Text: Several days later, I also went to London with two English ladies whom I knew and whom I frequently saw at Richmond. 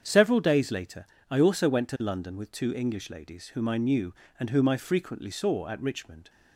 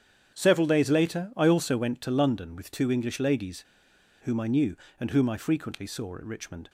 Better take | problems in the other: first | starts louder than the rest; strong; until 1.3 s; 8.5 dB; strong in the first // pauses between "ladies" and "whom"; noticeable; at 3.6 s; 0.58 s long

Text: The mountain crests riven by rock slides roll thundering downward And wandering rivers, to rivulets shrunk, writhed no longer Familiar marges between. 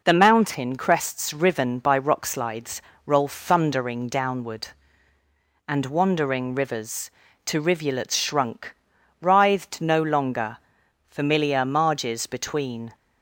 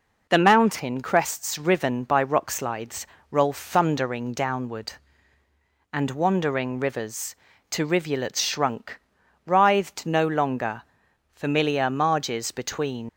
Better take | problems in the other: first | pauses between "slides" and "roll"; slight; at 3.0 s; 0.24 s long; slight in the first // pauses between "longer" and "Familiar"; noticeable; at 10.8 s; 0.54 s long; noticeable in the first // leaves "between" unfinished; at 13.0 s; 100 ms

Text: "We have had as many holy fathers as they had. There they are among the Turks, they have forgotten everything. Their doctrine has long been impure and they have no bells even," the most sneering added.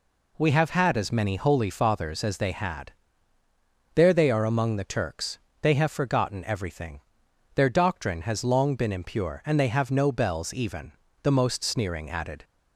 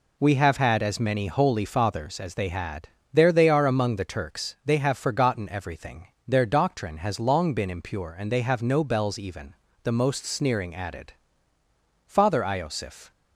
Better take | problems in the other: first | goes on to say "Father Iosif"; noticeable; from 12.0 s on; 1.0 s long

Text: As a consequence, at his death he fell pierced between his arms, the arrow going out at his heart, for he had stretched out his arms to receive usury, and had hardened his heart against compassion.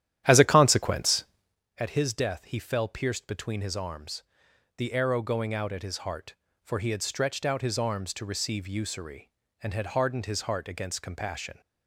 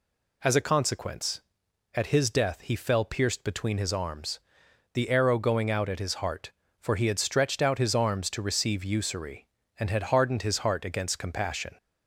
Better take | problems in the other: second | starts louder than the rest; strong; until 1.6 s; 11.5 dB

